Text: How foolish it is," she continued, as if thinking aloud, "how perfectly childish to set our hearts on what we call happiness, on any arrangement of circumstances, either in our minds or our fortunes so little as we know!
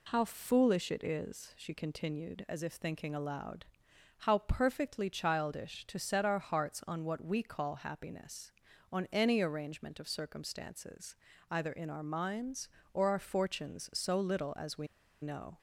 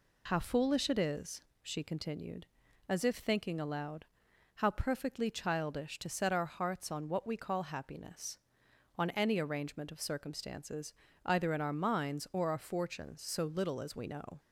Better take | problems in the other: second | pauses between "we" and "know"; slight; at 14.8 s; 0.35 s long

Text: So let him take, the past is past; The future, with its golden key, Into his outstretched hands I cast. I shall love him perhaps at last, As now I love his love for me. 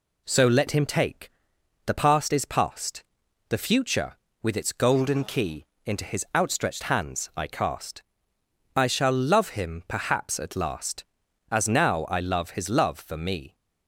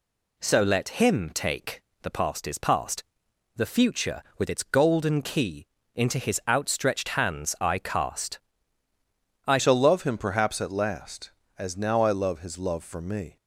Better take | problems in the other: first | changes voice at "shall"; from 9.5 s on; 3.8 s long

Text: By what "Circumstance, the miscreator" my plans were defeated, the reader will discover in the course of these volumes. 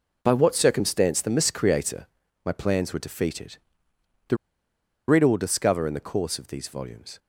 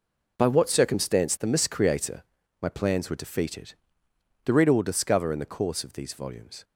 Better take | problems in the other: second | pauses between "miscreator" and "my"; at 2.0 s; 0.40 s long; also in the second // pauses between "the" and "reader"; noticeable; at 4.3 s; 0.71 s long

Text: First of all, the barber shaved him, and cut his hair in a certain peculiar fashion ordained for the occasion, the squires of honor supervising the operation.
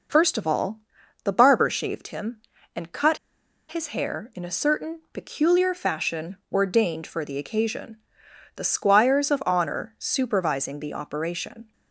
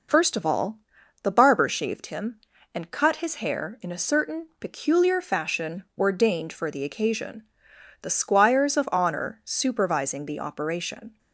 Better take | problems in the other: second | pauses between "cut" and "his"; noticeable; at 3.1 s; 0.52 s long // pauses between "fashion" and "ordained"; slight; at 6.3 s; 0.16 s long; slight in the second

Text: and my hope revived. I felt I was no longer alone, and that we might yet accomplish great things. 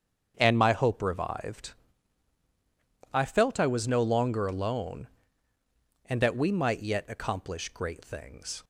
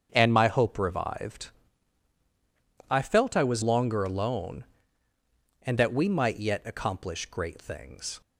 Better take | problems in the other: first | starts louder than the rest; strong; until 1.1 s; 7 dB; strong in the first // skips "no"; at 3.6 s

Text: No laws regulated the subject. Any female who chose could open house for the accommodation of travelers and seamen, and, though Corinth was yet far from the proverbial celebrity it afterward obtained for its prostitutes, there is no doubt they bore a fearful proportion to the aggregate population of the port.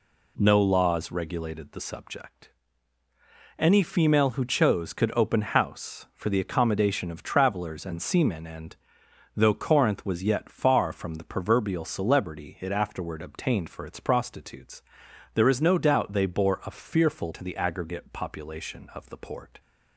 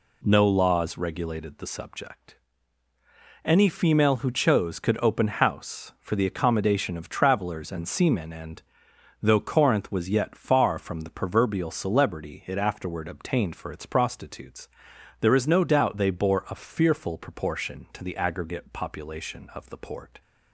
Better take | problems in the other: second | skips "proportion"; at 17.3 s

